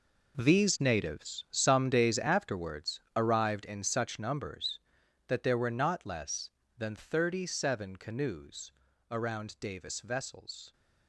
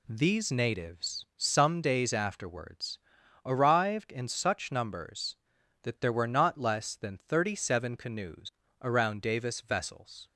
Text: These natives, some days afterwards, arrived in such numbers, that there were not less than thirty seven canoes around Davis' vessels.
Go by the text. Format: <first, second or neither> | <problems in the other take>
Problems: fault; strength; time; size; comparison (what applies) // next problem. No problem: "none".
second | gets quieter; strong; throughout; 13 dB // pauses between "canoes" and "around"; at 8.6 s; 0.40 s long; slight in the second